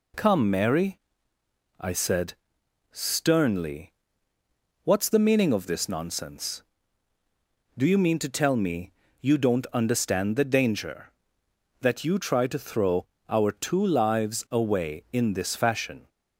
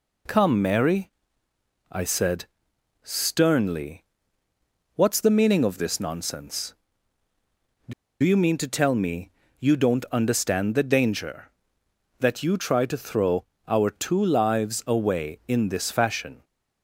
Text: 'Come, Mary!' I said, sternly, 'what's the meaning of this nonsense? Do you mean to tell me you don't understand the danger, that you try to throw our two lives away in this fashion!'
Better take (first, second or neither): first